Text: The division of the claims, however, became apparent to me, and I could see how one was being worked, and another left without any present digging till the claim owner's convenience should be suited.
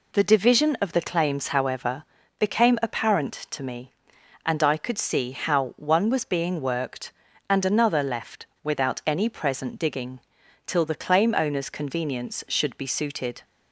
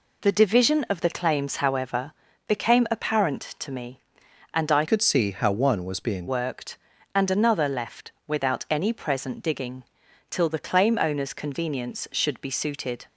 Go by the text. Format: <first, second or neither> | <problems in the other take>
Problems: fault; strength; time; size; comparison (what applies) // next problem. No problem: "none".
first | changes voice from "could" to "being"; from 4.8 to 6.2 s; 1.4 s long // pauses between "digging" and "till"; noticeable; at 9.8 s; 0.48 s long; noticeable in the first